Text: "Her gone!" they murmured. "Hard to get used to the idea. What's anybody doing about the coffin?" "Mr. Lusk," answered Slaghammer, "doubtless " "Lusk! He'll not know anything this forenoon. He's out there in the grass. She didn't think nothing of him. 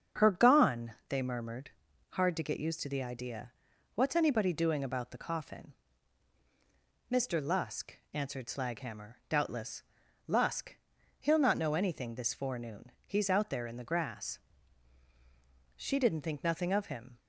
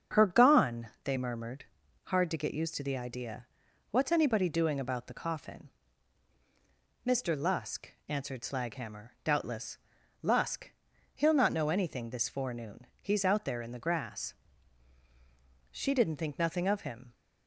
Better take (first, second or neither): neither